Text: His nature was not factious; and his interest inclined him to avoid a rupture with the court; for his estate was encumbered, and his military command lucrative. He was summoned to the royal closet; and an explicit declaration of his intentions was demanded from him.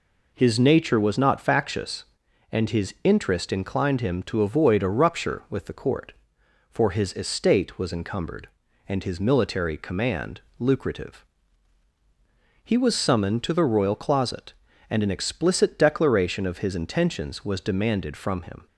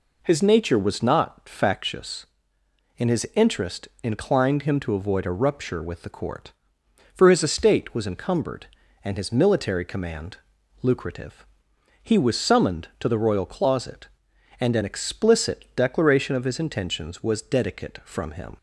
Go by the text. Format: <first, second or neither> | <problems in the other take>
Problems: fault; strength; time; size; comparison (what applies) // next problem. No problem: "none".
first | pauses between "command" and "lucrative"; noticeable; at 10.3 s; 0.46 s long; slight in the first // says "dedicate" for "demanded"; at 17.4 s